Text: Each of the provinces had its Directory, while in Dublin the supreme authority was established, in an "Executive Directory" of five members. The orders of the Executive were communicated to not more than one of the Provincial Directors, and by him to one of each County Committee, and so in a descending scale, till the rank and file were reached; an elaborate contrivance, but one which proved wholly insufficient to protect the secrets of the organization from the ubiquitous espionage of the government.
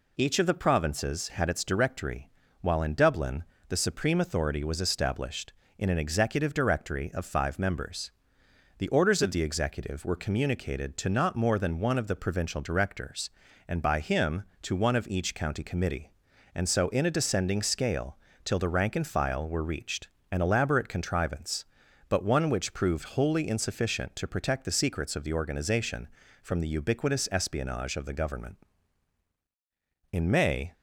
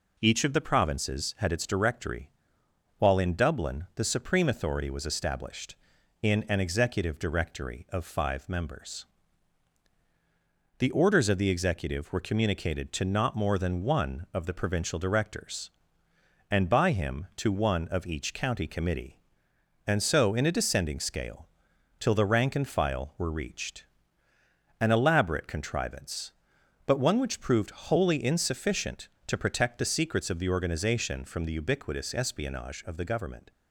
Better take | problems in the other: second | pauses between "Dublin" and "the"; slight; at 3.4 s; 0.26 s long // goes on to say "In May"; noticeable; from 30.1 s on; 0.62 s long

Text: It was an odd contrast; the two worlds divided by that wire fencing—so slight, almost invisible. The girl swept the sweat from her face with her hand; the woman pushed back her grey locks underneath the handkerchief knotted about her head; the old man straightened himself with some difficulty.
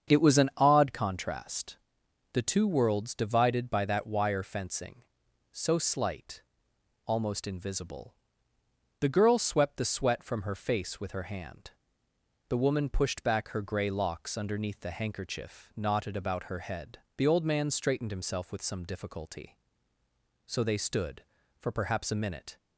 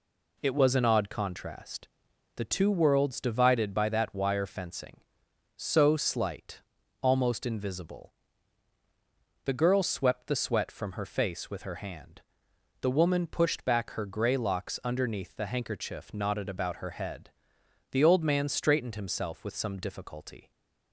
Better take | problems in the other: second | starts louder than the rest; strong; until 1.1 s; 7 dB // goes on to say "So they stood for perhaps a minute"; strong; from 20.4 s on; 2.1 s long

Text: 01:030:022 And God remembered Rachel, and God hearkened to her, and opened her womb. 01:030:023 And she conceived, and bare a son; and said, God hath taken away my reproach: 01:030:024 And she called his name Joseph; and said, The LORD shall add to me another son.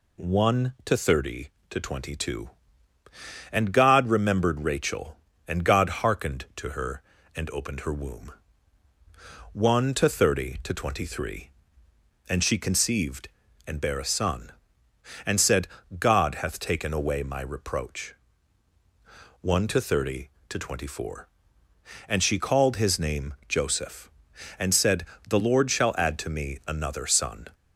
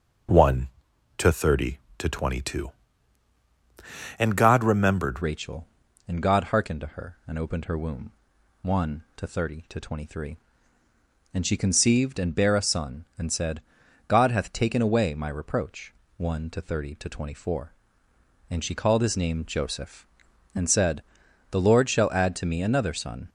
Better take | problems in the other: first | changes voice at "Rachel"; from 5.2 s on; 18.0 s long

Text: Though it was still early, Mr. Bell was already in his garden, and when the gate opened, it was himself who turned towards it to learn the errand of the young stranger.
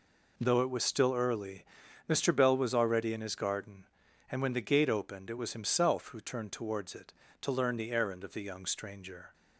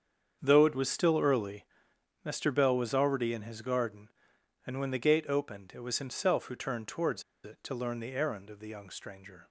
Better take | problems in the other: first | starts louder than the rest; strong; until 1.4 s; 7.5 dB // pauses between "towards" and "it"; slight; at 7.2 s; 0.23 s long

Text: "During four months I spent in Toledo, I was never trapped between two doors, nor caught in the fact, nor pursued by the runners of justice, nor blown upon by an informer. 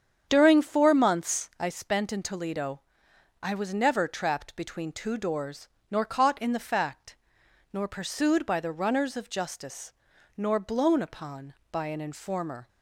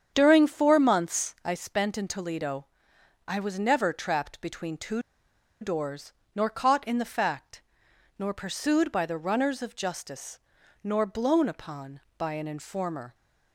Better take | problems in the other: first | starts louder than the rest; strong; until 1.1 s; 8 dB; strong in the first // pauses between "two" and "doors"; noticeable; at 5.0 s; 0.60 s long

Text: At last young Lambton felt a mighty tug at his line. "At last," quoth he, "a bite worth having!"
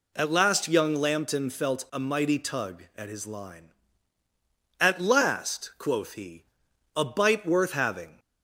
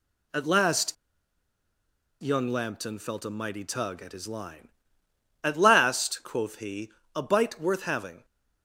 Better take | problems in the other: first | pauses between "last" and "young"; strong; at 0.9 s; 1.2 s long

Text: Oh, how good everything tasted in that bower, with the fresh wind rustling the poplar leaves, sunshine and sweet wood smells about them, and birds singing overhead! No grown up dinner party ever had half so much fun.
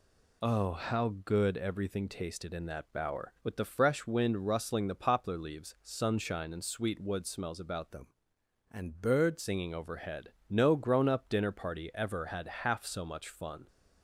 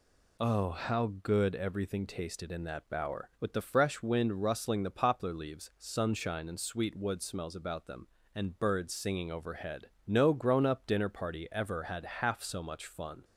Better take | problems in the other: second | changes voice from "them" to "birds"; from 7.9 to 9.3 s; 1.4 s long

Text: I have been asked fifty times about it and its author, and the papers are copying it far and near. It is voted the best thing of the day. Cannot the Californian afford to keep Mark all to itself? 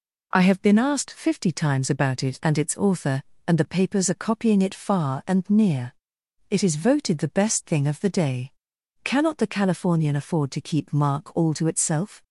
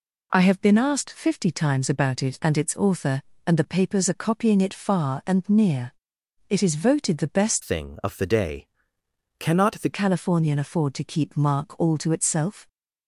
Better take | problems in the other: first | changes voice from "thing" to "the"; from 7.6 to 9.9 s; 2.3 s long

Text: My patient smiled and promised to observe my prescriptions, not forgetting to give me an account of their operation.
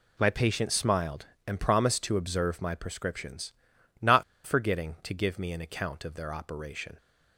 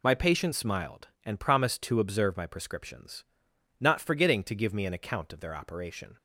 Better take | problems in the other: second | pauses between "not" and "forgetting"; slight; at 4.2 s; 0.23 s long

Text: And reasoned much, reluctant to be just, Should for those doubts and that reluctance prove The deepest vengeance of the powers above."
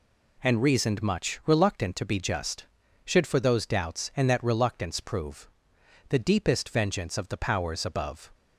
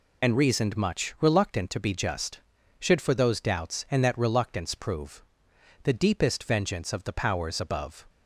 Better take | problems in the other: first | loses the start of "And"; at 0.2 s; 80 ms // pauses between "prove" and "The"; noticeable; at 5.2 s; 0.60 s long; noticeable in the first

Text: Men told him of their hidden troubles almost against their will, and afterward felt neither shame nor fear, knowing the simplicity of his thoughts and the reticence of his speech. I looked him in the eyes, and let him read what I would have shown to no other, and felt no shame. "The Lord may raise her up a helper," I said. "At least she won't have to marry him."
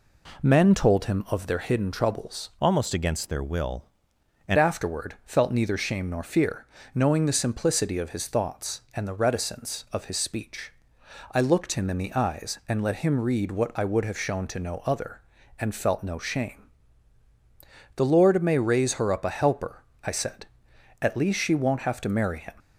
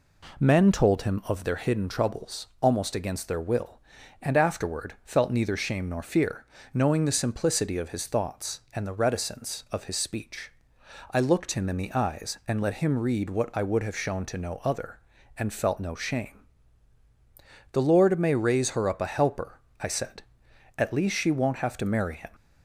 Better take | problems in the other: second | changes voice from "almost" to "and"; from 2.6 to 4.5 s; 1.9 s long

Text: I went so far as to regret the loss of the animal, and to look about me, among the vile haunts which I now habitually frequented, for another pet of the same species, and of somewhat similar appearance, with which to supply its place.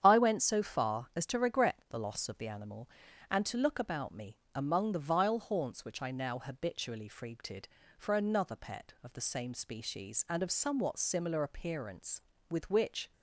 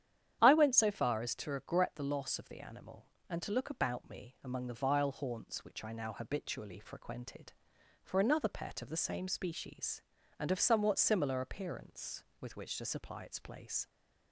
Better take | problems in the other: second | starts louder than the rest; strong; until 1.0 s; 9 dB; strong in the second // stops before "to supply its place"; at 13.1 s

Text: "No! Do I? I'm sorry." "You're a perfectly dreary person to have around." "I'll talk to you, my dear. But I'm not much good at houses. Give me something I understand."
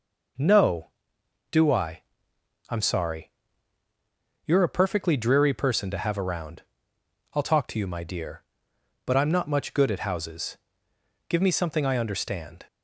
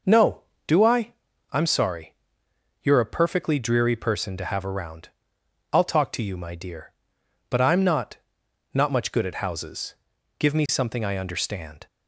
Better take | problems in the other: first | says "not" twice; at 8.7 s

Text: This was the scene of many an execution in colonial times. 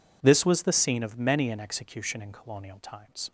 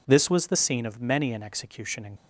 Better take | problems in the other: first | stops before "colonial times"; at 2.1 s

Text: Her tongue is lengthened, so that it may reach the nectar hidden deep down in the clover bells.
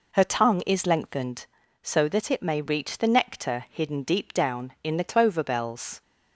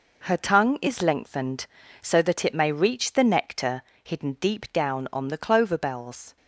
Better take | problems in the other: first | pauses between "nectar" and "hidden"; slight; at 3.8 s; 0.22 s long // says "on" for "in"; at 5.1 s

